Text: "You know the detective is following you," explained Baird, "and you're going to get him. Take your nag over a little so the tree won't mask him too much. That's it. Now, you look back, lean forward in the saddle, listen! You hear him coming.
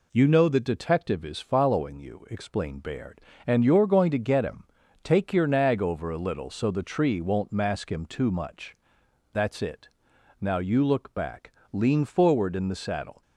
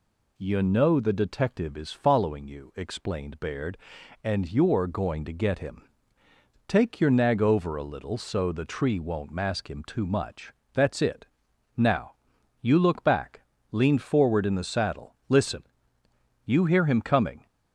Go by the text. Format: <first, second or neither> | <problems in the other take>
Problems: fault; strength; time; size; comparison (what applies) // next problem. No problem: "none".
second | stops before "listen You hear him coming"; at 13.2 s